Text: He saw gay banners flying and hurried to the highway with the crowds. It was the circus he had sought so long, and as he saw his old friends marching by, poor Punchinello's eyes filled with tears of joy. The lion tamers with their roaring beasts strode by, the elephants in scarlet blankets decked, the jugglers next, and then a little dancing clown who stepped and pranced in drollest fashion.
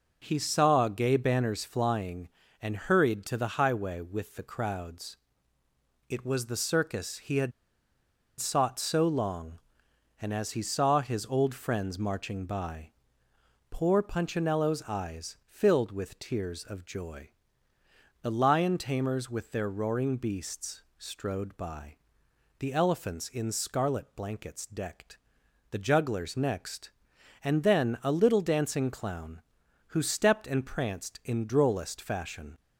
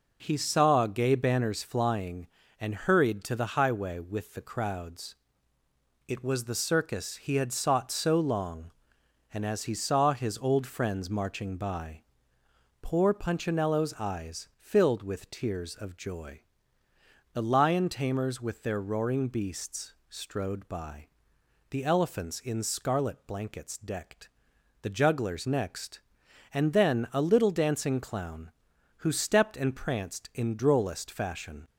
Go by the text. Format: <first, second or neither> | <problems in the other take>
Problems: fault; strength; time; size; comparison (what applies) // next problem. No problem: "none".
second | pauses between "had" and "sought"; noticeable; at 7.5 s; 0.87 s long // pauses between "beasts" and "strode"; slight; at 20.8 s; 0.16 s long; slight in the second